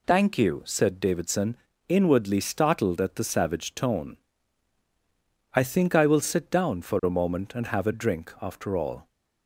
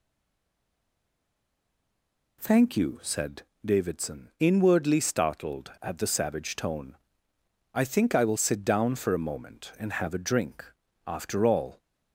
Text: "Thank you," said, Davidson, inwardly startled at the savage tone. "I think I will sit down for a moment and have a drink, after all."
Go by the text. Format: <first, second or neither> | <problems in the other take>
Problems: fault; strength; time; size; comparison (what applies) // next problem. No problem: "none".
first | stays silent before the first word; until 2.3 s; 2.3 s long